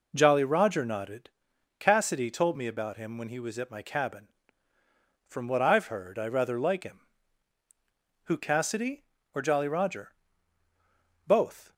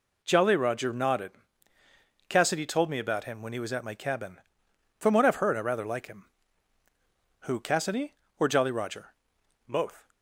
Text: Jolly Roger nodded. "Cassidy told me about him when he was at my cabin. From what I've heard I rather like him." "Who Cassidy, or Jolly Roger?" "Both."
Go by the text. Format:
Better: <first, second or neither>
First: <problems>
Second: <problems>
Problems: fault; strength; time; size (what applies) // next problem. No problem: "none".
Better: neither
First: none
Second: none